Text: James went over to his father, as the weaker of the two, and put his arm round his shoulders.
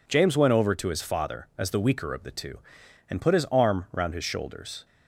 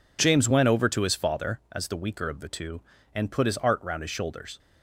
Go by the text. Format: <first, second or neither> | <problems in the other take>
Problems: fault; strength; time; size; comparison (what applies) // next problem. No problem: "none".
first | says "art" for "arm"; at 3.5 s